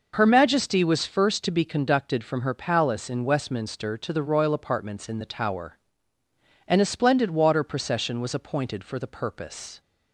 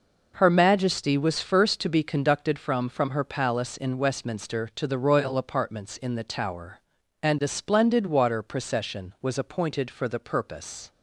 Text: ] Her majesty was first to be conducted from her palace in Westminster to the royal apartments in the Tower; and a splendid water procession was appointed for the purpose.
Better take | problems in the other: first | says "from" twice; at 2.8 s

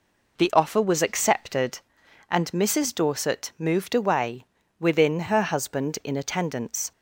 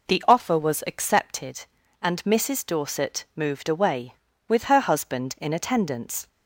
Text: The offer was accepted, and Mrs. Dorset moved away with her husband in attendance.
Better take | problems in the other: second | says "within" for "with"; at 4.7 s

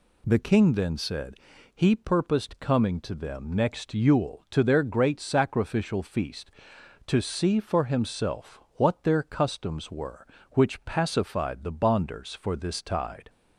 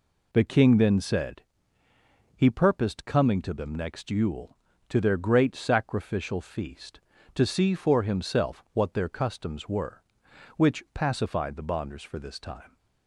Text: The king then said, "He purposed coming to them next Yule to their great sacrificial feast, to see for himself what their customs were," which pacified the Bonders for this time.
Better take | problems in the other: second | pauses between "himself" and "what"; slight; at 8.5 s; 0.18 s long // says "tide" for "time"; at 12.8 s

